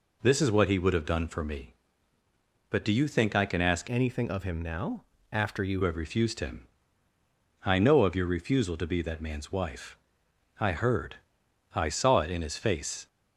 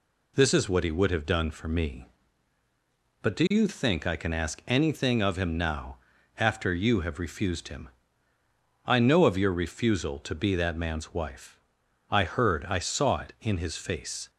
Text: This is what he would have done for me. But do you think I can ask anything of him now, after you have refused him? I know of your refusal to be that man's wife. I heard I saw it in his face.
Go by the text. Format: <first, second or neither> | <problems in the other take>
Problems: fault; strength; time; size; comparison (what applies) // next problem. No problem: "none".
second | changes voice from "anything" to "you"; from 3.8 to 5.8 s; 2.0 s long // pauses between "heard" and "I"; noticeable; at 11.1 s; 0.58 s long